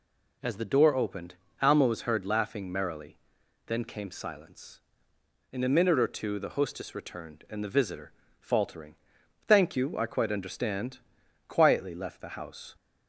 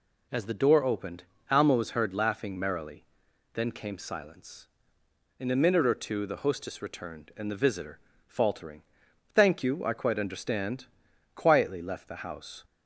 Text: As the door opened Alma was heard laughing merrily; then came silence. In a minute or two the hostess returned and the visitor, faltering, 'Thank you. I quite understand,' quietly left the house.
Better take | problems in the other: neither | pauses between "opened" and "Alma"; slight; the same in both

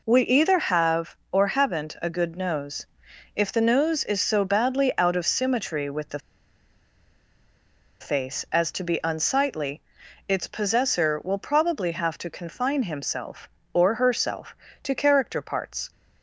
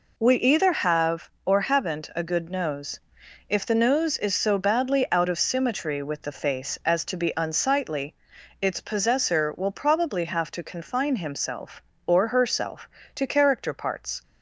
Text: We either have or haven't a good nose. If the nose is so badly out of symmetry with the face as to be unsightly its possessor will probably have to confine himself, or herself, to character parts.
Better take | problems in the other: second | pauses between "the" and "face"; strong; at 6.1 s; 1.8 s long // pauses between "unsightly" and "its"; noticeable; at 9.8 s; 0.46 s long; noticeable in the second

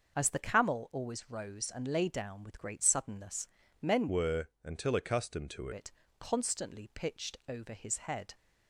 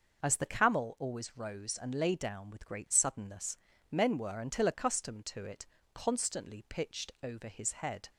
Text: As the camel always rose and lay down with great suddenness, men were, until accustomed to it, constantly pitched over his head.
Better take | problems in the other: second | changes voice from "were" to "to"; from 4.0 to 5.6 s; 1.6 s long

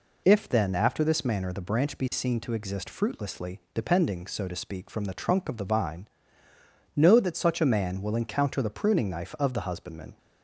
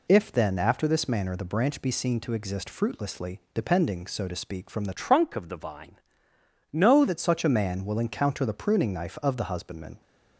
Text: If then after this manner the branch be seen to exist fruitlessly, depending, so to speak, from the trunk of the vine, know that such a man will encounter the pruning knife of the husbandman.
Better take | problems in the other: first | changes voice from "trunk" to "know"; from 4.9 to 7.0 s; 2.1 s long

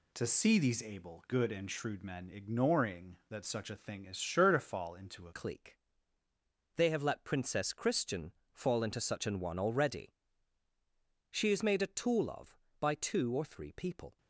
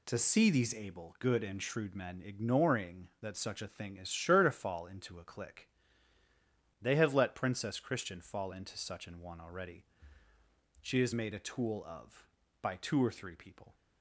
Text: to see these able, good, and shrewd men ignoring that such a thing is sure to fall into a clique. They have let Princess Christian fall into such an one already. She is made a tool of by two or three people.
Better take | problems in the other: second | changes voice at "clique"; from 5.3 s on; 8.8 s long // pauses between "Christian" and "fall"; slight; at 8.3 s; 0.20 s long

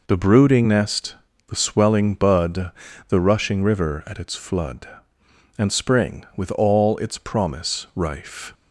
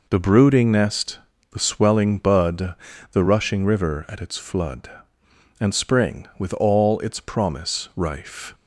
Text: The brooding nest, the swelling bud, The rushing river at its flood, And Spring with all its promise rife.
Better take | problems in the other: neither | none

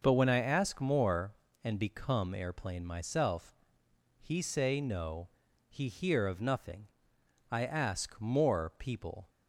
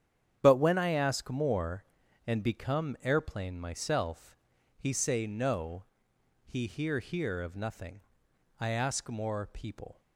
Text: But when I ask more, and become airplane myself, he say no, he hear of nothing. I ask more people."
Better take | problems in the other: first | starts louder than the rest; strong; until 1.4 s; 9 dB // says "hear" twice; at 6.9 s

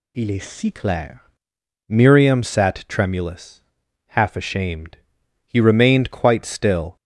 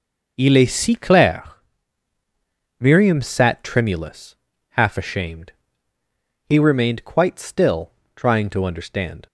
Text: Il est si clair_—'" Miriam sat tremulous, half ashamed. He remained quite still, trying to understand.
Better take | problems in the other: second | stops before "trying to understand"; at 6.9 s

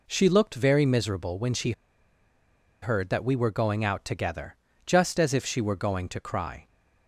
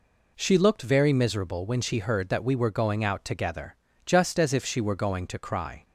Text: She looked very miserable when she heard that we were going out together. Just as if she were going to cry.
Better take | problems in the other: second | pauses between "she" and "heard"; at 1.7 s; 1.0 s long

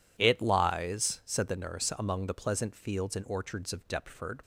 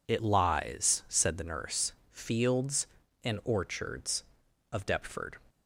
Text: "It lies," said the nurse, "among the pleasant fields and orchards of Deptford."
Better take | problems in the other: first | skips "among the pleasant"; at 2.0 s

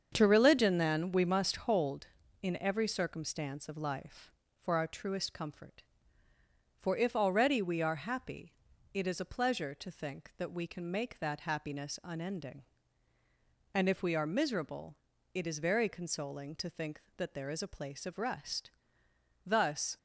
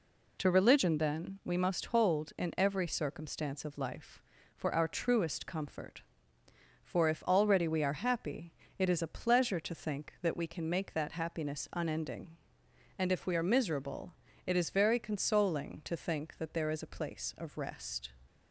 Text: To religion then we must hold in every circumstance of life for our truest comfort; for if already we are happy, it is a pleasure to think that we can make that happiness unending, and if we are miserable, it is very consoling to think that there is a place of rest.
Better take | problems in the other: second | starts louder than the rest; strong; until 1.1 s; 7 dB // goes on to say "Thus"; from 19.4 s on; 0.50 s long

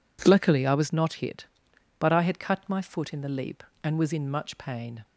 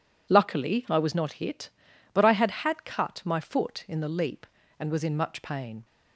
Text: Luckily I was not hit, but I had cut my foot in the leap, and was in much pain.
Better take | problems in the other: first | says "had" twice; at 2.4 s

